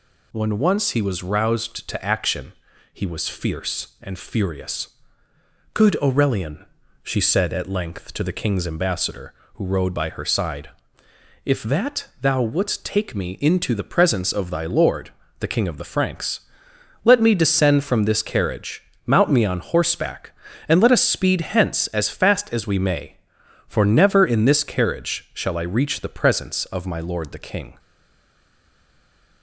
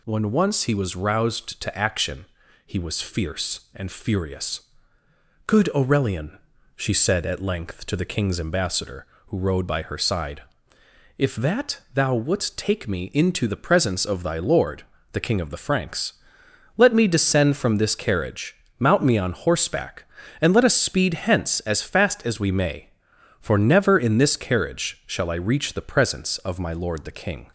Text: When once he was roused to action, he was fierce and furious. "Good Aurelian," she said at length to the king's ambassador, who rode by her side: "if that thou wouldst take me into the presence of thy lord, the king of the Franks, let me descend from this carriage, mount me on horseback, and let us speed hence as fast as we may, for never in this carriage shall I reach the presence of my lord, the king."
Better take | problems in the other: second | stays silent after the last word; noticeable; from 27.7 s on; 1.7 s long

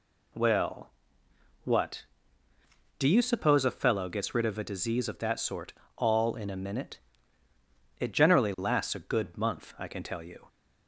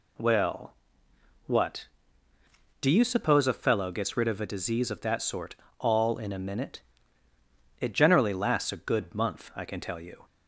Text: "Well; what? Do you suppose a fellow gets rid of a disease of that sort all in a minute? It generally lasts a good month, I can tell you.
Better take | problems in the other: neither | pauses between "sort" and "all"; slight; the same in both

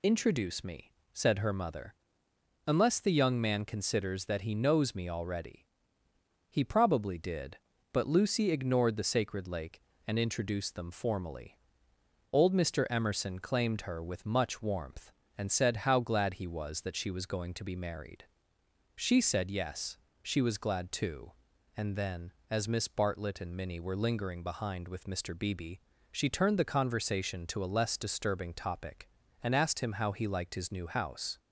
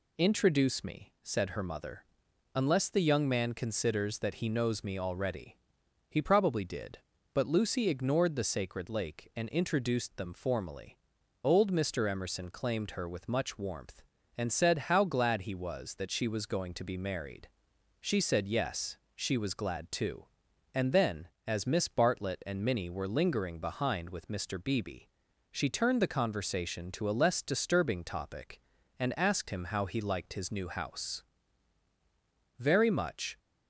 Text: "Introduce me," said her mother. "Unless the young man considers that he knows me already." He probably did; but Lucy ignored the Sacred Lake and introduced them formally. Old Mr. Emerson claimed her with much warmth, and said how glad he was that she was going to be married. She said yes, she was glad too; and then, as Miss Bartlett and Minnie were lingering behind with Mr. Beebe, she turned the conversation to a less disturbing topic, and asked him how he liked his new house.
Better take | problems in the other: first | goes on to say "Very much"; noticeable; from 32.5 s on; 0.80 s long

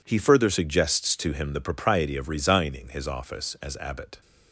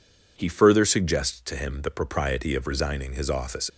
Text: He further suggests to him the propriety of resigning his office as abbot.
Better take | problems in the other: first | stops before "as abbot"; at 3.6 s

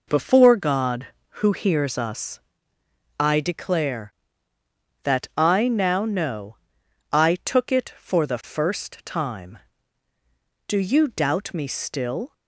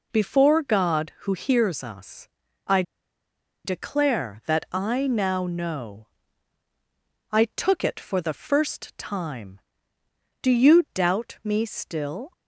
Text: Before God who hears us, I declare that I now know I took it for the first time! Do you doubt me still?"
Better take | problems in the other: first | pauses between "I" and "declare"; noticeable; at 2.8 s; 0.82 s long // pauses between "know" and "I"; at 6.0 s; 1.2 s long; noticeable in the first

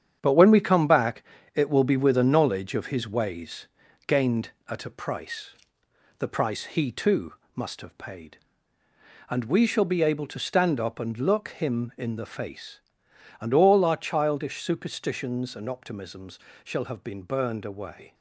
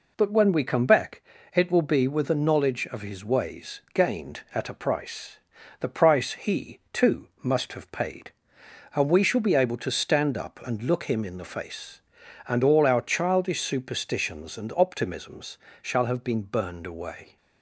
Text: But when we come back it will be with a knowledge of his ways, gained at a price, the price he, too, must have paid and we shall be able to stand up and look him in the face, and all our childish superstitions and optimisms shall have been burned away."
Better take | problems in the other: second | gets quieter; strong; throughout; 8 dB // pauses between "back" and "it"; slight; at 1.2 s; 0.30 s long; slight in the second // pauses between "optimisms" and "shall"; slight; at 16.3 s; 0.26 s long; slight in the second

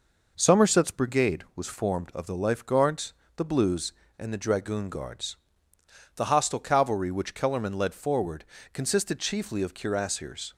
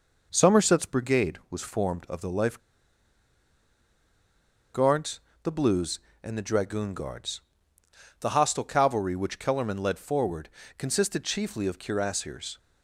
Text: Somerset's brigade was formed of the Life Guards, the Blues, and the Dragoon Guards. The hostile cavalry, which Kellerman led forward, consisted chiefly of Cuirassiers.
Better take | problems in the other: first | pauses between "Life" and "Guards"; strong; at 2.5 s; 2.1 s long

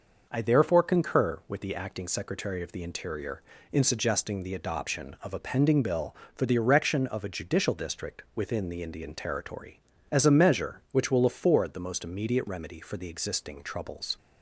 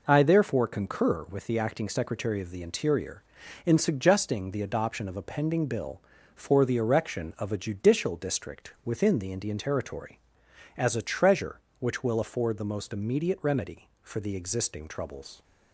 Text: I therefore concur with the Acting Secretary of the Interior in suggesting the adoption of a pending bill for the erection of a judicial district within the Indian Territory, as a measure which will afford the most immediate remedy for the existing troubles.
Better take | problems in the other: first | says "treasure" for "measure"; at 11.0 s

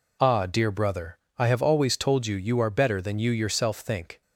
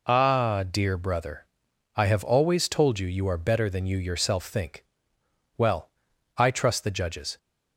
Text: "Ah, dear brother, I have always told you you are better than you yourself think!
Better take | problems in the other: first | goes on to say "Well I trust the judges"; strong; from 5.5 s on; 1.8 s long

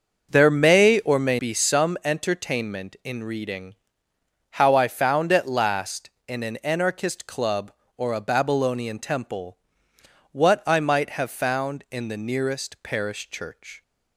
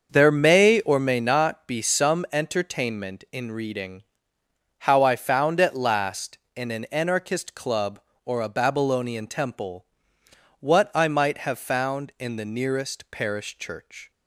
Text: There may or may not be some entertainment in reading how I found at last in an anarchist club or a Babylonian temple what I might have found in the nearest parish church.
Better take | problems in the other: second | starts louder than the rest; until 1.3 s; 6.5 dB; also in the second // skips "not"; at 1.3 s // pauses between "reading" and "how"; noticeable; at 3.7 s; 0.78 s long; noticeable in the second // pauses between "temple" and "what"; noticeable; at 9.5 s; 0.72 s long; noticeable in the second

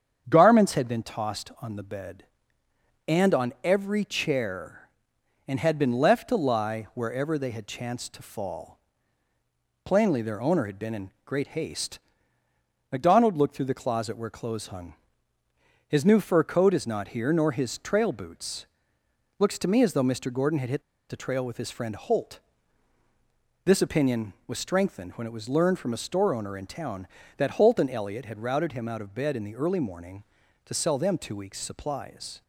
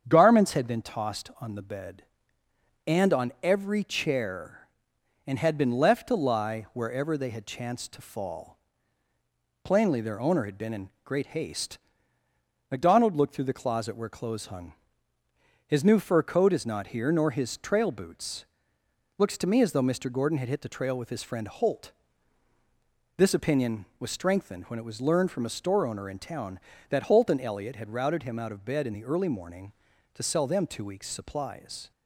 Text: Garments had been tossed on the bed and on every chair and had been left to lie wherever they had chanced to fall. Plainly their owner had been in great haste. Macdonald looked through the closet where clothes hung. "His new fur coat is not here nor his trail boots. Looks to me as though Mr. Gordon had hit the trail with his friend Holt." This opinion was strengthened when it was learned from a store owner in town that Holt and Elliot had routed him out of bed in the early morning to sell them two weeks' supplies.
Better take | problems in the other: second | starts louder than the rest; strong; until 1.2 s; 8 dB; strong in the second // pauses between "hit" and "the"; slight; at 20.8 s; 0.27 s long

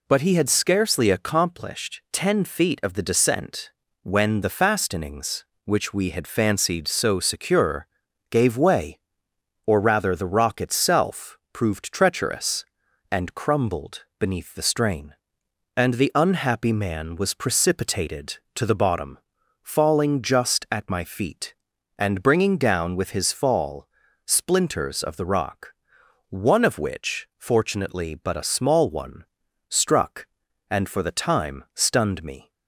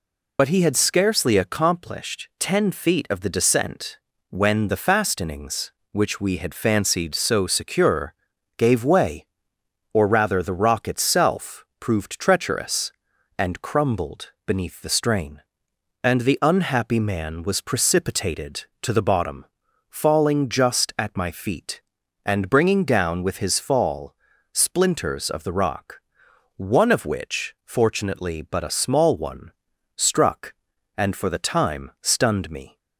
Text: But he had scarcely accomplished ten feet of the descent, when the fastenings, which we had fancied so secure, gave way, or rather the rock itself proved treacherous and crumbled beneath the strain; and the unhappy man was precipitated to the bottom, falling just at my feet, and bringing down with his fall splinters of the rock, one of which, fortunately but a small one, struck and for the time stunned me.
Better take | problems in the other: first | loses the start of "But"; at 0.3 s; 50 ms // pauses between "crumbled" and "beneath"; slight; at 14.3 s; 0.16 s long; slight in the first // pauses between "fall" and "splinters"; slight; at 24.1 s; 0.36 s long; slight in the first

